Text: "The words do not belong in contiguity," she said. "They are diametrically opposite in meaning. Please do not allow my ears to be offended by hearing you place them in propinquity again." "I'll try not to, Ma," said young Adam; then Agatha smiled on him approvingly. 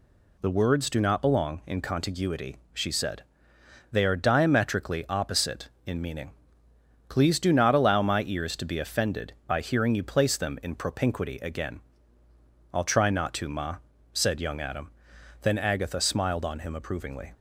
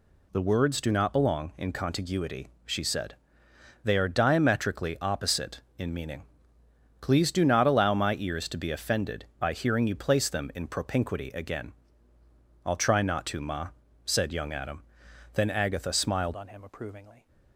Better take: first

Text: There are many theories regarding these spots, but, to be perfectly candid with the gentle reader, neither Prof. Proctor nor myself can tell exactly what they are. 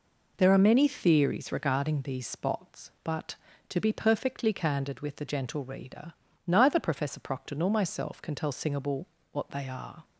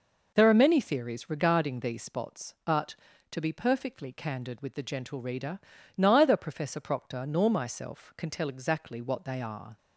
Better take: second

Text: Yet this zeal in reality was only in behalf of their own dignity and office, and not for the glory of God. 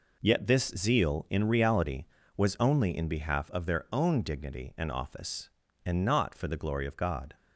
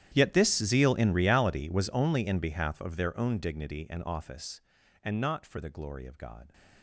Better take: first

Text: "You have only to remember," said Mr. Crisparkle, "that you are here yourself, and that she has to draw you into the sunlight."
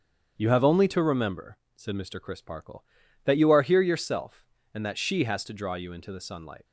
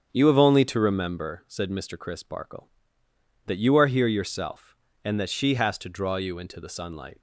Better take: neither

